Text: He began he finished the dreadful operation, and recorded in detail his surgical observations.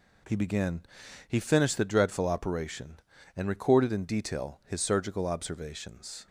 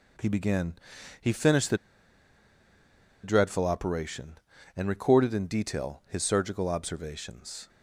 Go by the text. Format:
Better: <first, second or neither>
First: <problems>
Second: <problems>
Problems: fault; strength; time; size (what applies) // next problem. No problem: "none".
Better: first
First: pauses between "began" and "he"; noticeable; at 0.8 s; 0.46 s long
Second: pauses between "began" and "he"; noticeable; at 0.7 s; 0.46 s long // pauses between "the" and "dreadful"; strong; at 1.7 s; 1.4 s long